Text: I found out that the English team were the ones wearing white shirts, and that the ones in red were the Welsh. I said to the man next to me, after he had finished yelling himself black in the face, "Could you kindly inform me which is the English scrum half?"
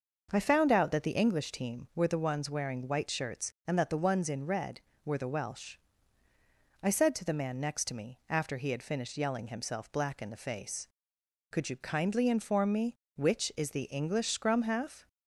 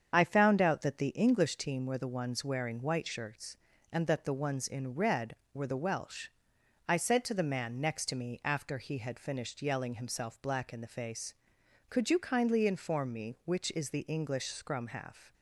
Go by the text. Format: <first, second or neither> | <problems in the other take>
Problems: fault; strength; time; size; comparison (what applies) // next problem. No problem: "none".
first | loses the start of "I"; at 0.1 s; 40 ms // starts louder than the rest; strong; until 1.1 s; 7.5 dB; also in the first